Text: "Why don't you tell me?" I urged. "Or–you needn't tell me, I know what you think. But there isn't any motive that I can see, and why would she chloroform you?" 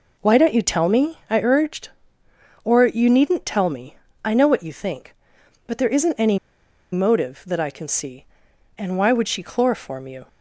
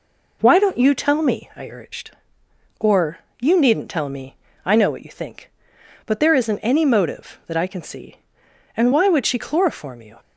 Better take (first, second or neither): second